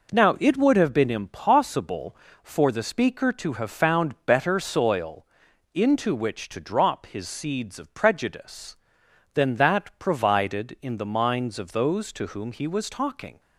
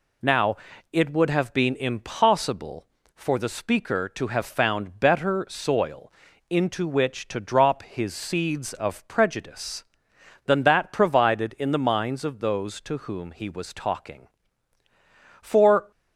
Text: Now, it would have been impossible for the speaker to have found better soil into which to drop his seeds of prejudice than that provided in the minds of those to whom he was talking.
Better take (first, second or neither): first